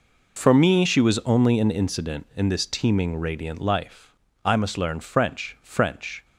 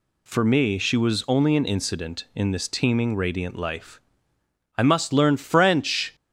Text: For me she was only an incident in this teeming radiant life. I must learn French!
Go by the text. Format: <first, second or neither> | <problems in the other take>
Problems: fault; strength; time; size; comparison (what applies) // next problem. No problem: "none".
second | says "French" twice; at 5.6 s